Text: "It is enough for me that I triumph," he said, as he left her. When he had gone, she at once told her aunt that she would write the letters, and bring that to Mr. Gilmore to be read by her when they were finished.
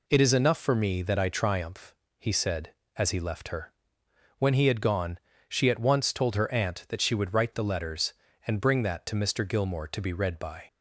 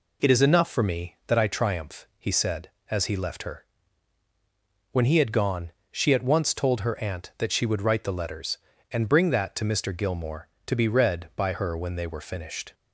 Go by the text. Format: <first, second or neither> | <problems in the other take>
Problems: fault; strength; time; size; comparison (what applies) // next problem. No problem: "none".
second | stops before "her when they were finished"; at 10.6 s